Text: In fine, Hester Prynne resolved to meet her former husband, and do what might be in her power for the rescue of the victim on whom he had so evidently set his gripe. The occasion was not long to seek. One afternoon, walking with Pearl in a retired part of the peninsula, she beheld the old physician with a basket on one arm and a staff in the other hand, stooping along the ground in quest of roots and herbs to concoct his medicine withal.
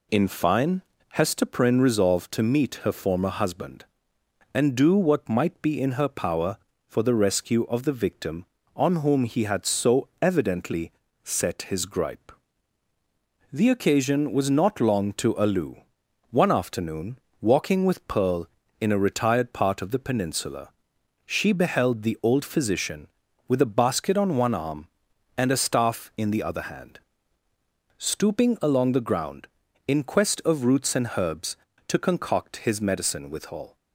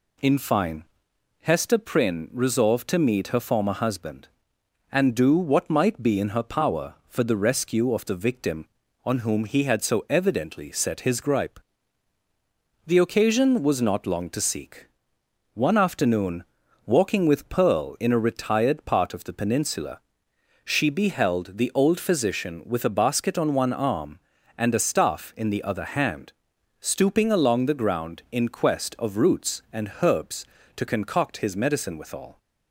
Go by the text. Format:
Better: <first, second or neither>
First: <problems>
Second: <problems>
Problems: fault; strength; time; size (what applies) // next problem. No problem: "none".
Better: second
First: pauses between "evidently" and "set"; slight; at 10.9 s; 0.32 s long // says "alu" for "seek"; at 15.3 s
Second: none